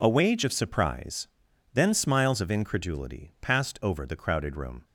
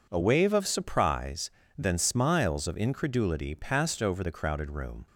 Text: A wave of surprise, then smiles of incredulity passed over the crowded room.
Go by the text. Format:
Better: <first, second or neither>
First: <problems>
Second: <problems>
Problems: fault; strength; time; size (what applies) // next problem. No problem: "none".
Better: second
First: says "wage" for "wave"; at 0.0 s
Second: none